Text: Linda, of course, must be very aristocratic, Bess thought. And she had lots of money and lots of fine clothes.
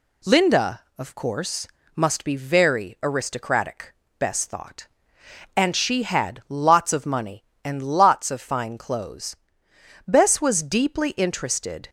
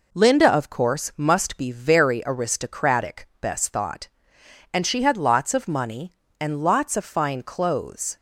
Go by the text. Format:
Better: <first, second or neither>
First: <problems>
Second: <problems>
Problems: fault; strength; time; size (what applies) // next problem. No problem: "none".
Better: second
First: goes on to say "Bess was deeply interested"; strong; from 10.0 s on; 1.8 s long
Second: none